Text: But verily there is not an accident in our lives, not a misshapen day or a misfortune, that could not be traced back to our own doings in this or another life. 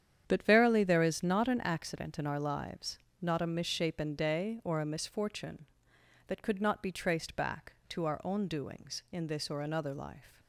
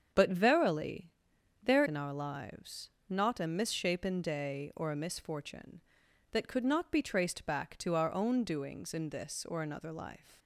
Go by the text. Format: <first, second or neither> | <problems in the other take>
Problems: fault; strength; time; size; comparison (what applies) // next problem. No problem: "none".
first | starts louder than the rest; strong; until 1.6 s; 7.5 dB; strong in the first // pauses between "verily" and "there"; noticeable; at 1.1 s; 0.52 s long // skips "is not an accident"; at 1.8 s